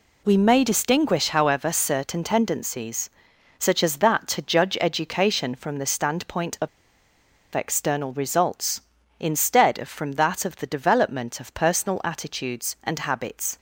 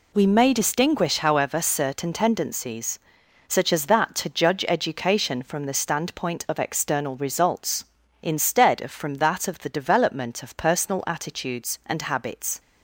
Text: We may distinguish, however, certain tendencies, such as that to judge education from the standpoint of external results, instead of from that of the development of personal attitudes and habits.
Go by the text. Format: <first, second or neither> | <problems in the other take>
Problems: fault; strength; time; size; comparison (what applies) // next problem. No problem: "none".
second | pauses between "of" and "external"; noticeable; at 6.6 s; 0.86 s long